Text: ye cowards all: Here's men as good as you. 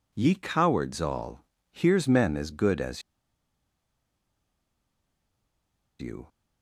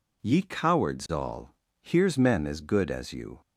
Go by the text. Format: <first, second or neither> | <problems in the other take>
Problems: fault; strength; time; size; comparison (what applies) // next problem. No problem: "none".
second | pauses between "as" and "you"; strong; at 3.0 s; 2.9 s long